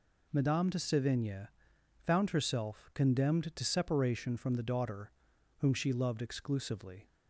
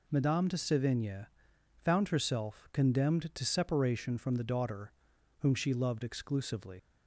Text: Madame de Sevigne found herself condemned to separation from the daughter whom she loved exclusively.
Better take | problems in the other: first | pauses between "Sevigne" and "found"; noticeable; at 1.2 s; 0.54 s long; noticeable in the first // pauses between "daughter" and "whom"; noticeable; at 4.9 s; 0.48 s long; noticeable in the first // leaves "exclusively" unfinished; at 6.7 s; 95 ms

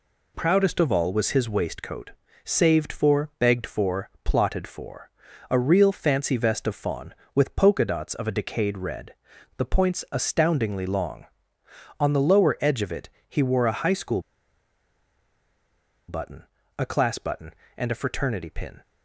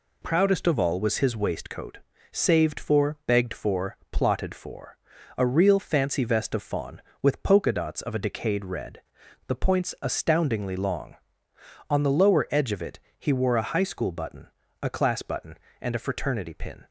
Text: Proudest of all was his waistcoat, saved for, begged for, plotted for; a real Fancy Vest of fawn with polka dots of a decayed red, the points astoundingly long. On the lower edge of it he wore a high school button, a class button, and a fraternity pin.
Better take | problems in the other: second | pauses between "it" and "he"; slight; at 13.0 s; 0.22 s long; slight in the second // pauses between "school" and "button"; strong; at 14.1 s; 1.8 s long

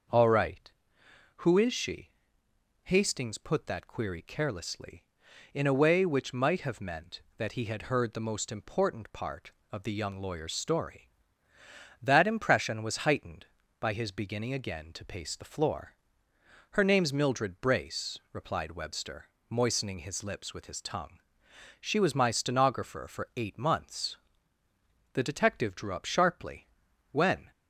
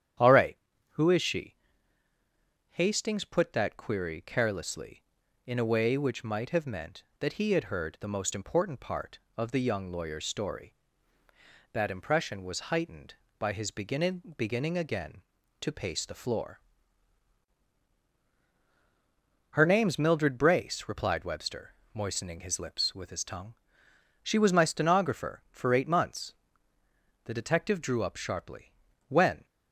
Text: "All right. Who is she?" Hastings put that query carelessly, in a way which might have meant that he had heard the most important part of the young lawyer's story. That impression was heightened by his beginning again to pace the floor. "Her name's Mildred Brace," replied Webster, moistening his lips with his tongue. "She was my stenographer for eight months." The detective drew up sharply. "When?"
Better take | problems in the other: first | starts louder than the rest; strong; until 1.5 s; 9.5 dB; also in the first // says "beginning" twice; at 14.3 s

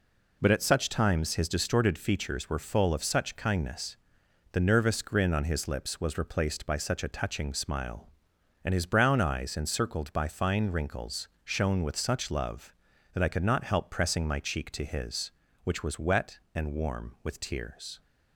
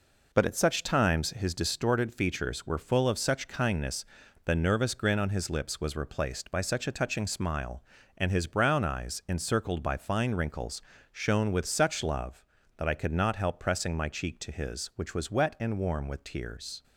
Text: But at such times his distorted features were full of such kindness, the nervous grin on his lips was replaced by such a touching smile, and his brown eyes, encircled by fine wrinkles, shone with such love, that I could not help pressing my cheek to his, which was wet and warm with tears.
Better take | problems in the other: neither | none

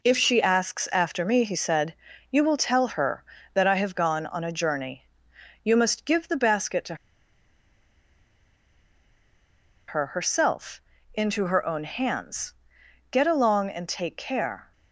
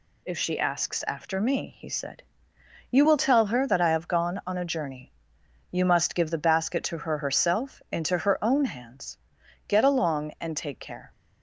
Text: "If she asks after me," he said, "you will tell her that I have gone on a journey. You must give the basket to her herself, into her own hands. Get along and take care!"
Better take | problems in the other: second | pauses between "to" and "her"; strong; at 6.9 s; 2.9 s long

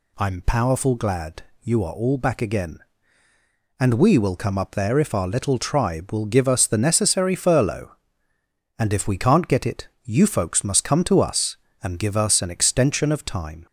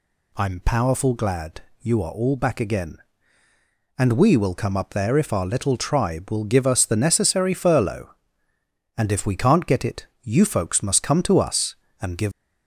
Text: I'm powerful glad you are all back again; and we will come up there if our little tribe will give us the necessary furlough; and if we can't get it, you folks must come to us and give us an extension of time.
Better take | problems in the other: first | pauses between "glad" and "you"; slight; at 1.6 s; 0.22 s long; slight in the first // stops before "us an extension of time"; at 12.3 s

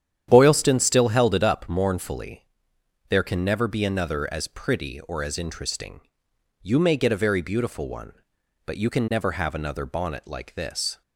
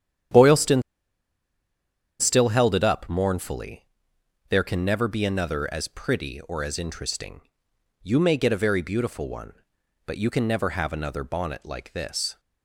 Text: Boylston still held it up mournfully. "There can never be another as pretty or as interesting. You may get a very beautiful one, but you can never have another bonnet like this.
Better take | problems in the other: first | starts louder than the rest; strong; until 2.7 s; 9.5 dB; strong in the first // pauses between "Boylston" and "still"; strong; at 0.8 s; 1.3 s long

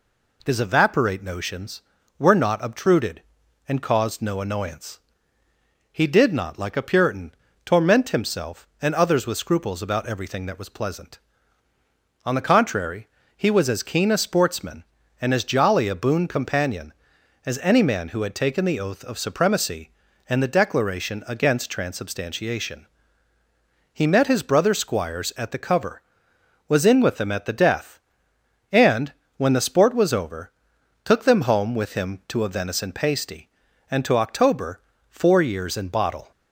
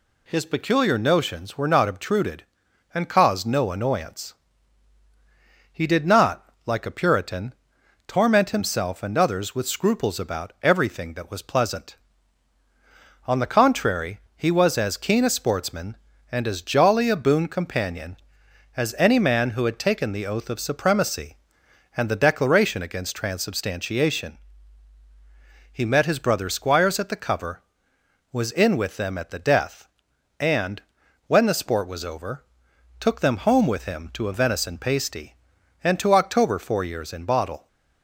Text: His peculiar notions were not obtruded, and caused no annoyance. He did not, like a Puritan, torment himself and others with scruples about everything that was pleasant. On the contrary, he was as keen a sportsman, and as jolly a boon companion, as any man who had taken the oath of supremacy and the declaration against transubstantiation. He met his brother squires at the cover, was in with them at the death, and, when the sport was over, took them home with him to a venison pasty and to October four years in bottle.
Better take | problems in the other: second | says "evaporate" for "peculiar"; at 0.5 s // pauses between "October" and "four"; slight; at 34.7 s; 0.30 s long

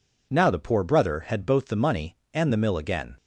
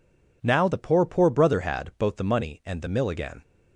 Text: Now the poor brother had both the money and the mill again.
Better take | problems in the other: first | says "poor" twice; at 1.0 s

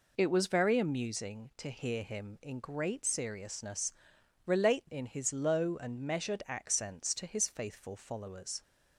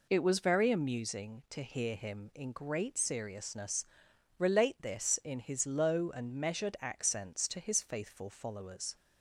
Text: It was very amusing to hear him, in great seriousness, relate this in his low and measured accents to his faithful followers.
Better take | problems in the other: second | skips "this"; at 4.9 s

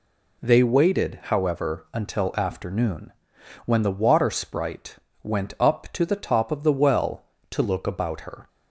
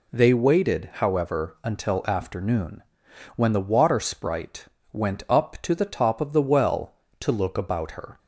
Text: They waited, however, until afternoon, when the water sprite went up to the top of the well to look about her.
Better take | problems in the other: neither | pauses between "sprite" and "went"; slight; the same in both

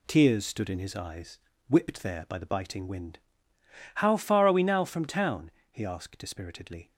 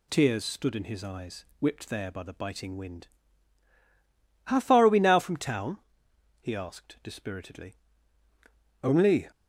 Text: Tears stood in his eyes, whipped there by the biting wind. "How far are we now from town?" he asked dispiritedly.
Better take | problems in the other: first | goes on to say "Only"; slight; from 8.8 s on; 0.46 s long

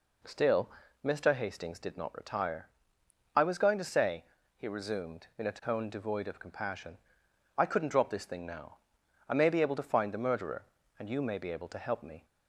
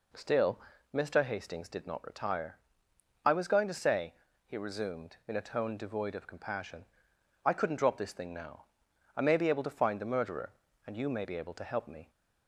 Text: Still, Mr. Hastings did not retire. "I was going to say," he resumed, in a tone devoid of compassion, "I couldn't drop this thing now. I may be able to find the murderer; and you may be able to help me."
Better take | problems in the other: neither | none

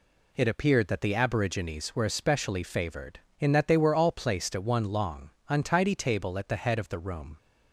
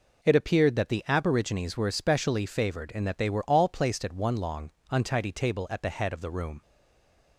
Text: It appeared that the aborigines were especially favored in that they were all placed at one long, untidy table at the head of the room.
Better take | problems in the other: first | stays silent after the last word; slight; from 6.6 s on; 0.7 s long

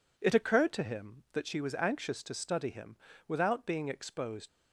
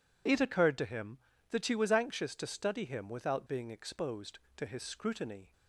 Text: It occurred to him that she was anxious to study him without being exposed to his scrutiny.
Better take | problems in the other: second | pauses between "him" and "without"; slight; at 2.9 s; 0.30 s long // stops before "to his scrutiny"; at 4.4 s

